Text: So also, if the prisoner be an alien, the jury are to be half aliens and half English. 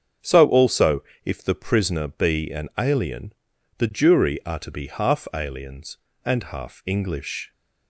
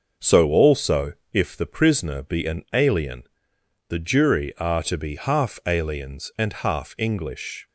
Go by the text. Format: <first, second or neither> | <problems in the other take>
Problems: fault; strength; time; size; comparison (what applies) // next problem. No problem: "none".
neither | starts louder than the rest; the same in both